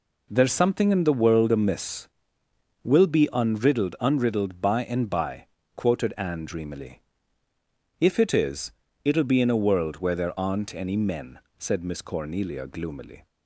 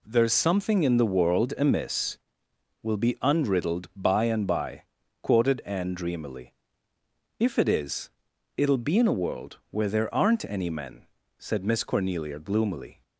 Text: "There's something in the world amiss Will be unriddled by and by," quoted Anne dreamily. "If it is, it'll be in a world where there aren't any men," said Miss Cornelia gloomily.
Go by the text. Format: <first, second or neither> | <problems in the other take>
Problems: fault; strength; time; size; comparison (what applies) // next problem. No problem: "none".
second | says "unriddled" twice; at 3.9 s